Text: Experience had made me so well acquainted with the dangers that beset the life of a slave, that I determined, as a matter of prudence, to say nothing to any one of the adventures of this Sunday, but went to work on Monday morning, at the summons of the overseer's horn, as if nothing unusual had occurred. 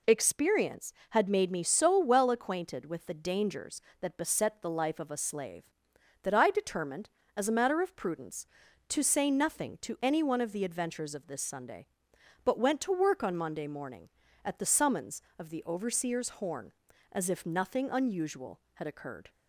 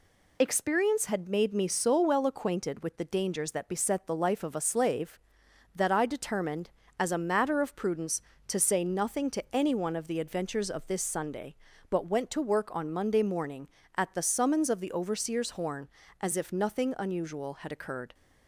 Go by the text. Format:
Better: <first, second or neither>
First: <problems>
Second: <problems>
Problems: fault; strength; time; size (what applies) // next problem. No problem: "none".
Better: neither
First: none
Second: none